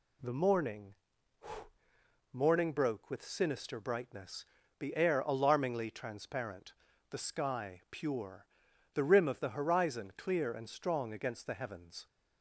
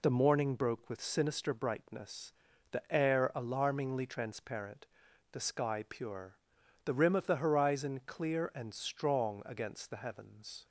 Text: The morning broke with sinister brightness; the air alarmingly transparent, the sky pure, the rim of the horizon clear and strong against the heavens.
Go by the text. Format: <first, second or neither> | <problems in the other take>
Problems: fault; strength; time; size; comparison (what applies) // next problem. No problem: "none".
second | says "morning" twice; at 2.3 s